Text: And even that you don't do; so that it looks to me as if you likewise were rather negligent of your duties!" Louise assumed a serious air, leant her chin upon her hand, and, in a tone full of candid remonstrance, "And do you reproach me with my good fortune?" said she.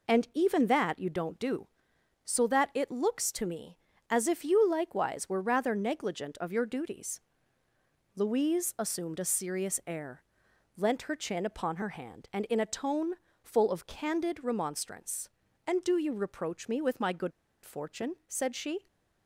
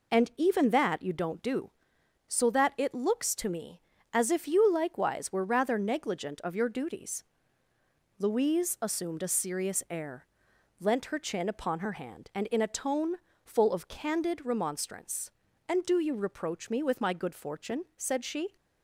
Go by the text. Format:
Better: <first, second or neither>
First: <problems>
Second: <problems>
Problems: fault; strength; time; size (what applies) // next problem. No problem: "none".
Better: second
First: pauses between "tone" and "full"; slight; at 13.1 s; 0.32 s long // pauses between "good" and "fortune"; slight; at 17.3 s; 0.32 s long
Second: pauses between "tone" and "full"; slight; at 13.1 s; 0.32 s long